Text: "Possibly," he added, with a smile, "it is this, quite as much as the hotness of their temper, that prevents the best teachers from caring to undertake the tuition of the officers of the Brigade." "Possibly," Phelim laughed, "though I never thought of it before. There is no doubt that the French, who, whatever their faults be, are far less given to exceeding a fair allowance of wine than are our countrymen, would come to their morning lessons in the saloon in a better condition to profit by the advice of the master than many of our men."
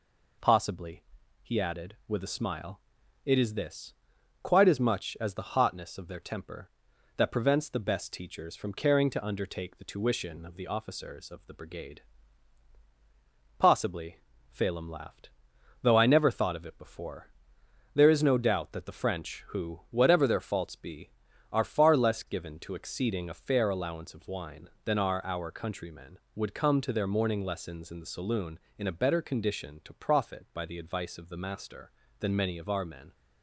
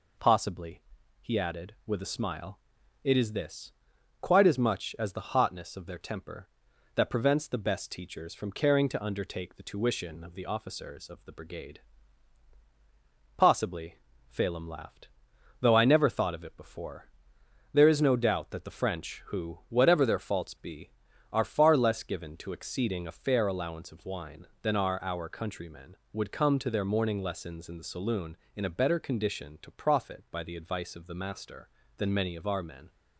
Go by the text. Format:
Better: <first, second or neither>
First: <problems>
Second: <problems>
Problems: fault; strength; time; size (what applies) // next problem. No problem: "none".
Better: neither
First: none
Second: none